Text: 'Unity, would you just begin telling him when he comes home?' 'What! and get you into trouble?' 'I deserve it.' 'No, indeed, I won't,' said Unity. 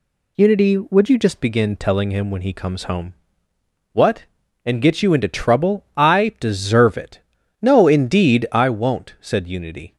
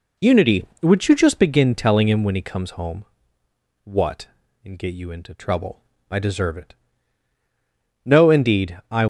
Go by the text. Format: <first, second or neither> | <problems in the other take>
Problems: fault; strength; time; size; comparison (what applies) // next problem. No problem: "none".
first | stops before "won't said Unity"; at 9.0 s